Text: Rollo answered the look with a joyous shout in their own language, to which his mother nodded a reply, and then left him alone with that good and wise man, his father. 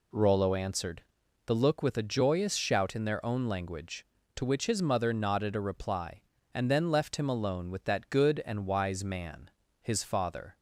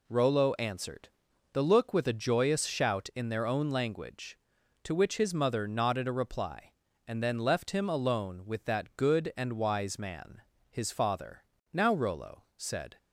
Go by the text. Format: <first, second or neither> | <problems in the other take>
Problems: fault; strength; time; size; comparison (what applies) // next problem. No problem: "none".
first | pauses between "answered" and "the"; at 1.0 s; 0.44 s long; also in the first // goes on to say "Now Rollo said"; noticeable; from 11.7 s on; 1.2 s long